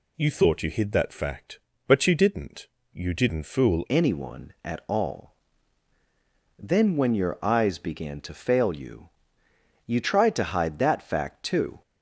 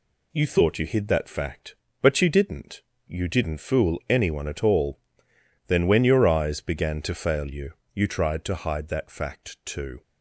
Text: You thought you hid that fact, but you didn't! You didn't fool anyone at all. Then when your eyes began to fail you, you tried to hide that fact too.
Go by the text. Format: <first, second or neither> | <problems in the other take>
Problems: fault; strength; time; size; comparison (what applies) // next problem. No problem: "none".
second | changes voice at "anyone"; from 3.8 s on; 8.0 s long